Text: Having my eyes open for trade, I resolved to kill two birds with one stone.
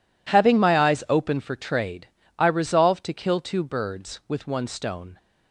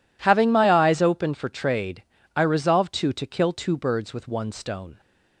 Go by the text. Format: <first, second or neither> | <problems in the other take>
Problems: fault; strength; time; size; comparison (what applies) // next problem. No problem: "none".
first | says "to" twice; at 3.1 s